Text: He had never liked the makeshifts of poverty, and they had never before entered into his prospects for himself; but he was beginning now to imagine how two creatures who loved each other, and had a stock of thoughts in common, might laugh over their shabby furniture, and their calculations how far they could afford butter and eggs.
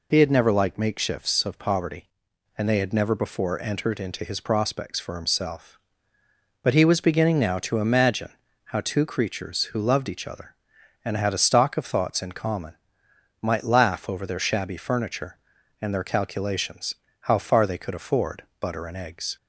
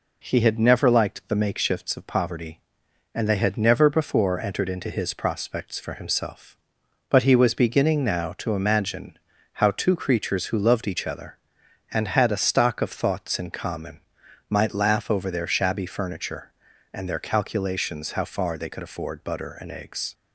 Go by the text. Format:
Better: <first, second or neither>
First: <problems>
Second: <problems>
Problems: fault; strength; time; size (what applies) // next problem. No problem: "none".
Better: second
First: skips "the"; at 0.7 s // pauses between "imagine" and "how"; slight; at 8.3 s; 0.32 s long // pauses between "calculations" and "how"; slight; at 16.9 s; 0.34 s long // pauses between "afford" and "butter"; slight; at 18.4 s; 0.16 s long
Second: pauses between "imagine" and "how"; slight; at 9.1 s; 0.36 s long